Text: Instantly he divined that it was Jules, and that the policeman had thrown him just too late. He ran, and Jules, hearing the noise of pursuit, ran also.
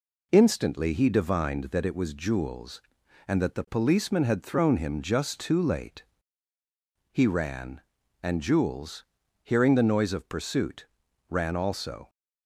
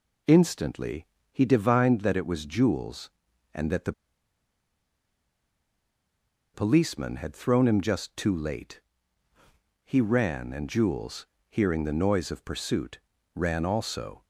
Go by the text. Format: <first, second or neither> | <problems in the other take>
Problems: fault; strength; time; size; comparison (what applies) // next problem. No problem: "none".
first | pauses between "Instantly" and "he"; slight; at 1.0 s; 0.26 s long // pauses between "the" and "policeman"; strong; at 3.9 s; 2.6 s long